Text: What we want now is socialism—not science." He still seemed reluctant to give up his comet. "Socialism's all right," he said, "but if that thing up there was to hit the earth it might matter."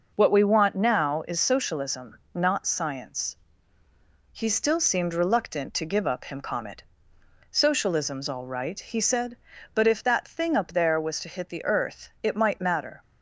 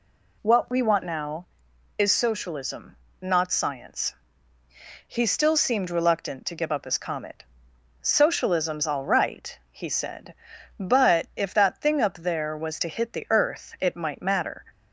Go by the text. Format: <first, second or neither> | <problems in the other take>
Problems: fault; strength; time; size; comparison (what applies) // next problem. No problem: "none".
second | says "him" for "his"; at 6.2 s